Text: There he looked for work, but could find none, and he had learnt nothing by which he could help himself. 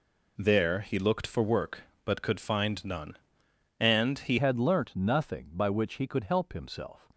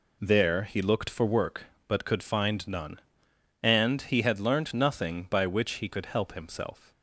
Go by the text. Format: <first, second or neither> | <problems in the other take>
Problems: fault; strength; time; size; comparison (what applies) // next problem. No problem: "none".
second | changes voice at "had"; from 4.3 s on; 2.7 s long